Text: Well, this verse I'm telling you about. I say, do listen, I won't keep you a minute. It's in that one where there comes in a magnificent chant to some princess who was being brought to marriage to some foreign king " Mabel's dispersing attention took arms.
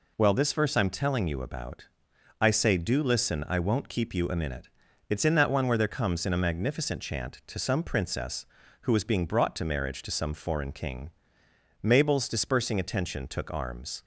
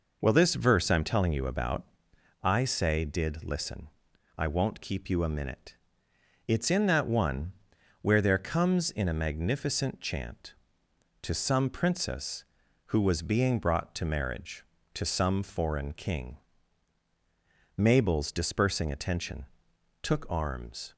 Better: first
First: none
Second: says "did" for "do"; at 3.0 s // pauses between "one" and "where"; noticeable; at 7.5 s; 0.50 s long // pauses between "attention" and "took"; noticeable; at 19.4 s; 0.58 s long

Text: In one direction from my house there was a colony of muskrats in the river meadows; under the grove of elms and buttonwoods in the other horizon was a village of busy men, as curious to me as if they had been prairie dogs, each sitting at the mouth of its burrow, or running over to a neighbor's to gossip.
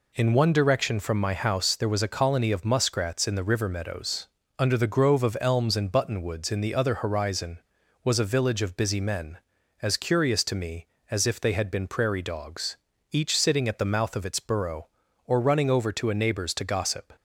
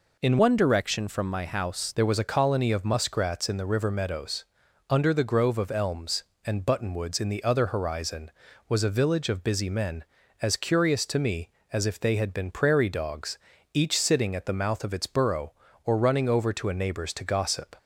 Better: first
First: none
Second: changes voice from "one" to "house"; from 0.3 to 1.9 s; 1.6 s long

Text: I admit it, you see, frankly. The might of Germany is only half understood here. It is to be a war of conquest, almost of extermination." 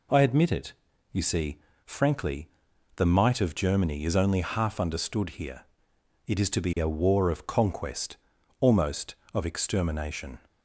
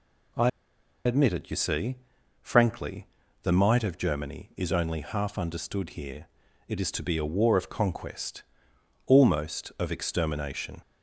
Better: first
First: none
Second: pauses between "I" and "admit"; noticeable; at 0.4 s; 0.56 s long

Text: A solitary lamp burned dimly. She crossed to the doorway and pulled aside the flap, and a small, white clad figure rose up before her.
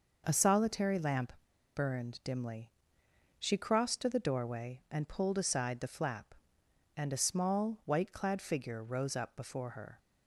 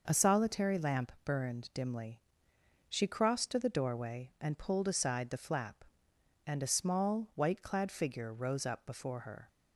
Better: second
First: pauses between "lamp" and "burned"; at 1.3 s; 0.41 s long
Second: none

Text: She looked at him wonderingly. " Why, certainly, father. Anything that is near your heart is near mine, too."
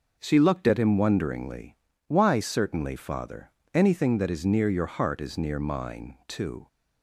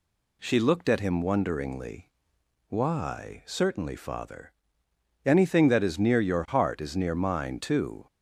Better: neither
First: none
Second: none

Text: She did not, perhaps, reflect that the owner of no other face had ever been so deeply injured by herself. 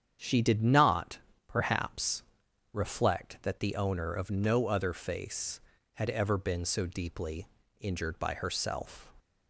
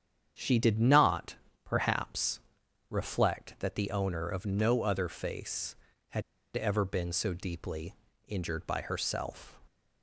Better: first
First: starts louder than the rest; strong; until 1.5 s; 8.5 dB // pauses between "deeply" and "injured"; slight; at 7.4 s; 0.32 s long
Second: starts louder than the rest; strong; until 1.6 s; 8.5 dB // pauses between "had" and "ever"; slight; at 6.2 s; 0.34 s long // pauses between "deeply" and "injured"; slight; at 7.9 s; 0.32 s long

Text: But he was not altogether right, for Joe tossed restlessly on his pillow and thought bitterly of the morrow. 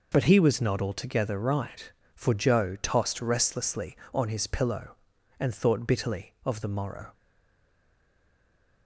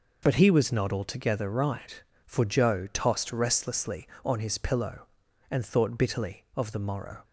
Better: second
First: stays silent after the last word; noticeable; from 7.1 s on; 1.7 s long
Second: none

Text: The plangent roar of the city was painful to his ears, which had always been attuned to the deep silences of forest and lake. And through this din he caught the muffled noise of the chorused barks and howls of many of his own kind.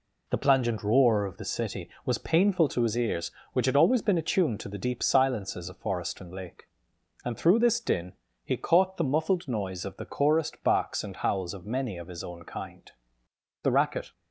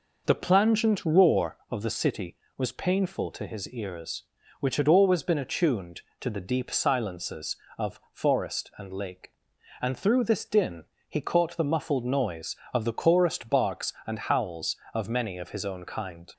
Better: second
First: pauses between "din" and "he"; slight; at 8.1 s; 0.30 s long // goes on to say "The racket"; from 13.6 s on; 0.50 s long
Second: pauses between "din" and "he"; slight; at 10.8 s; 0.24 s long

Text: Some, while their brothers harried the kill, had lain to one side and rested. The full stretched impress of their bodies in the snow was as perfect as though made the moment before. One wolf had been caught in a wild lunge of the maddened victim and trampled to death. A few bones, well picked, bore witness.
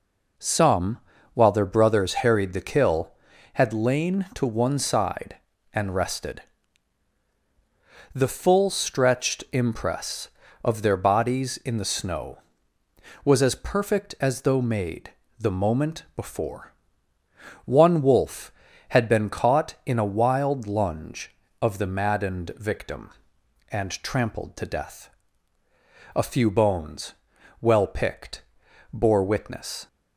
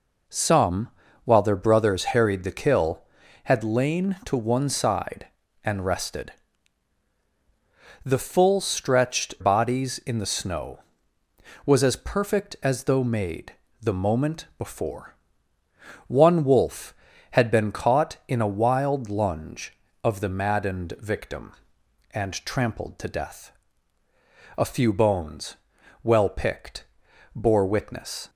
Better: first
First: pauses between "made" and "the"; slight; at 15.1 s; 0.28 s long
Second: skips "impress of their"; at 9.3 s // pauses between "made" and "the"; slight; at 13.5 s; 0.28 s long

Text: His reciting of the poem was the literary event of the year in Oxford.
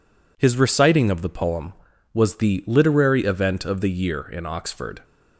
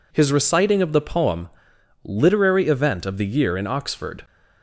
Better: first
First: none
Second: skips "was the"; at 1.7 s

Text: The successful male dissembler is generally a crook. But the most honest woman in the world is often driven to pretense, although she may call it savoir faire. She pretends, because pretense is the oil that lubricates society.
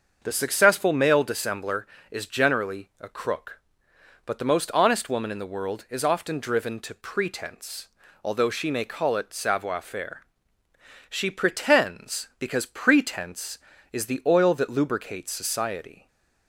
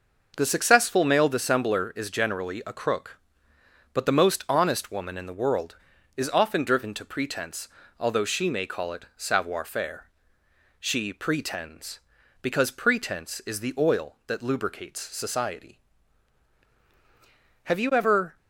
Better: first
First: starts louder than the rest; until 1.2 s; 6.5 dB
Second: starts louder than the rest; noticeable; until 1.3 s; 6 dB // goes on to say "Have you ever"; noticeable; from 17.6 s on; 0.71 s long

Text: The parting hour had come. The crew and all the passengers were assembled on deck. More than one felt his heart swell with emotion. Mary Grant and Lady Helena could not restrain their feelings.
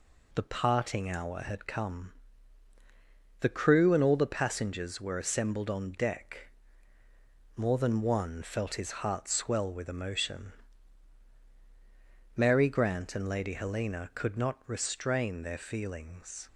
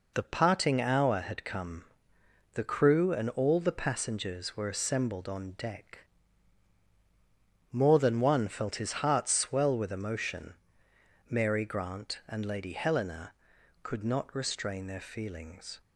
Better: neither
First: none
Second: none

